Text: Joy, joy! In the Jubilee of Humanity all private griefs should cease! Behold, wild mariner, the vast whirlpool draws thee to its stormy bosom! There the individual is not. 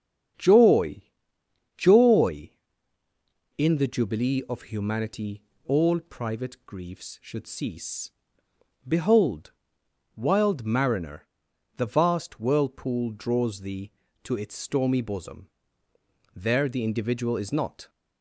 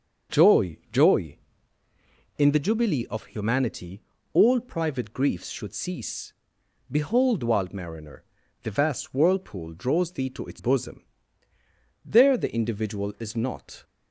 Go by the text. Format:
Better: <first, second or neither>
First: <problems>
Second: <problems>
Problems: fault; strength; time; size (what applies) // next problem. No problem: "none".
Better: first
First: starts louder than the rest; strong; until 2.1 s; 8 dB // pauses between "Humanity" and "all"; slight; at 5.4 s; 0.22 s long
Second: starts louder than the rest; until 2.5 s; 6.5 dB // pauses between "Humanity" and "all"; slight; at 4.0 s; 0.32 s long // skips "stormy"; at 10.5 s